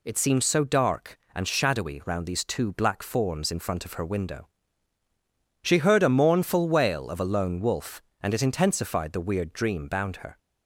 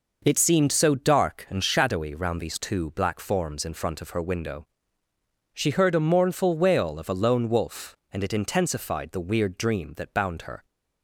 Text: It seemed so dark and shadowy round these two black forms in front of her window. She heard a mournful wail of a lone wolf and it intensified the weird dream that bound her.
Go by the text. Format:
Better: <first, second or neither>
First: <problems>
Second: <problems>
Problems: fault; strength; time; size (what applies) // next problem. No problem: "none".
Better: second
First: skips "that"; at 9.8 s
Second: none